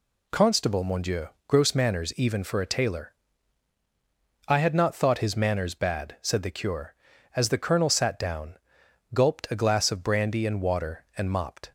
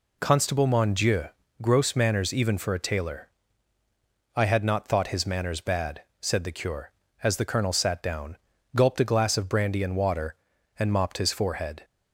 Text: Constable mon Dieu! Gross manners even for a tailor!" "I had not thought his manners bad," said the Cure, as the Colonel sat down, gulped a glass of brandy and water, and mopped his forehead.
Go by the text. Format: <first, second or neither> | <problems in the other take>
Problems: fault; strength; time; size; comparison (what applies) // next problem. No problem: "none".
second | stops before "his forehead"; at 11.6 s